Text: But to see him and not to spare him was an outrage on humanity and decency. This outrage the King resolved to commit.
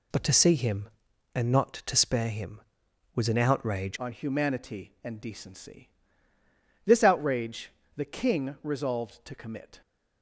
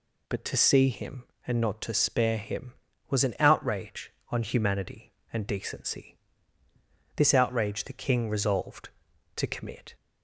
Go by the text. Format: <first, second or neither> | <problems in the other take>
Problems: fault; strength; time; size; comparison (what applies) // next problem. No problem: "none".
second | changes voice at "on"; from 3.9 s on; 5.9 s long // pauses between "outrage" and "the"; slight; at 7.7 s; 0.24 s long